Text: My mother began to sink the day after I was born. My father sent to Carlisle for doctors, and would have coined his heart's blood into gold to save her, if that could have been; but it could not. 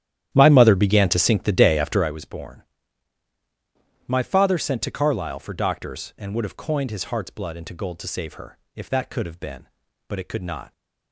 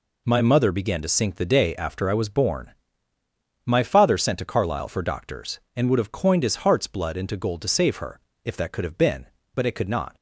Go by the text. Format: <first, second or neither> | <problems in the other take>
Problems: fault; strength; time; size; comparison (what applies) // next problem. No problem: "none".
second | starts louder than the rest; strong; until 2.2 s; 11 dB